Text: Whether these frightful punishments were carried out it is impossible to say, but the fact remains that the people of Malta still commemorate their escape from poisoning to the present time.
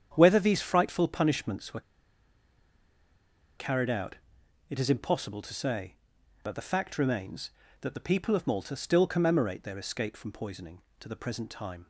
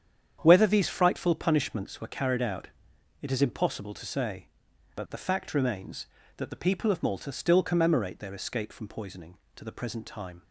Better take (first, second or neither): second